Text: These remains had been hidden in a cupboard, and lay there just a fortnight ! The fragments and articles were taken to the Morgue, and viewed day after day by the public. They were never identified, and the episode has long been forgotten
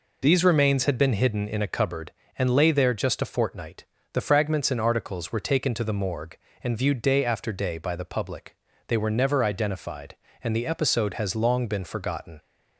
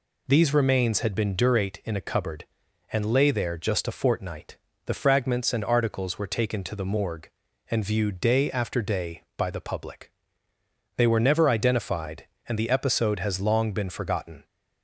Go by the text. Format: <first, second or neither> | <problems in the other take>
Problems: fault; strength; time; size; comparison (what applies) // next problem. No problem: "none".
first | says "durate" for "hidden"; at 1.3 s